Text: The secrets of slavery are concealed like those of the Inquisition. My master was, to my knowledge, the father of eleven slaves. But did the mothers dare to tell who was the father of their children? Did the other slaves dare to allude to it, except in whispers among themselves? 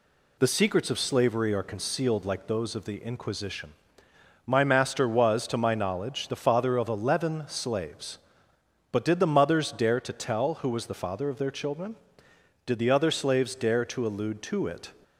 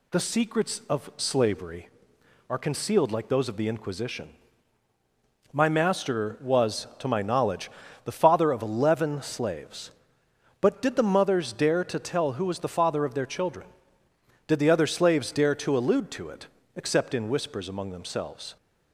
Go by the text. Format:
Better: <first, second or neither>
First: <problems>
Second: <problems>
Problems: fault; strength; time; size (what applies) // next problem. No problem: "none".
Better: second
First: stops before "except in whispers among themselves"; at 15.0 s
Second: none